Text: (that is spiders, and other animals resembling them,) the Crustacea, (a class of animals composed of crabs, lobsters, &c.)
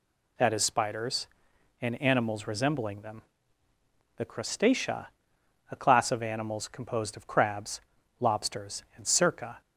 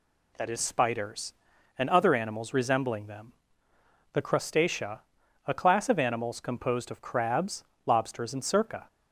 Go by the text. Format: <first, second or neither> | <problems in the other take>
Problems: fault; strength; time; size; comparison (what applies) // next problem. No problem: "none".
second | skips "other"; at 2.0 s